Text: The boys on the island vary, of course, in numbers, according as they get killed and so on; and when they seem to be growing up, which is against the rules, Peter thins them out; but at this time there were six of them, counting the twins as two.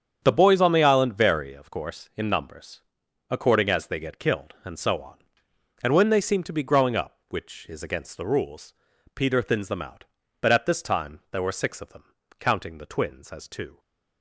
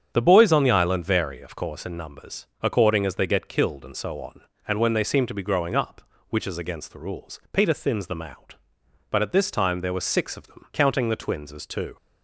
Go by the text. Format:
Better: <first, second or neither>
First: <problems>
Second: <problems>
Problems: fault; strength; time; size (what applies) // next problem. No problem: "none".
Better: neither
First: starts louder than the rest; strong; until 1.2 s; 8 dB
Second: starts louder than the rest; strong; until 1.1 s; 8 dB